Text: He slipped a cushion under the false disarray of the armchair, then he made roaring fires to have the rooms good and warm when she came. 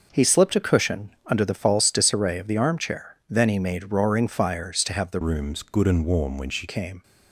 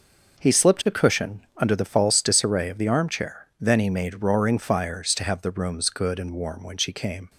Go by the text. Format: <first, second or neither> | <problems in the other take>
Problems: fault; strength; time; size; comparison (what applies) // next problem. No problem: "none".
second | changes voice from "rooms" to "she"; from 5.2 to 6.6 s; 1.4 s long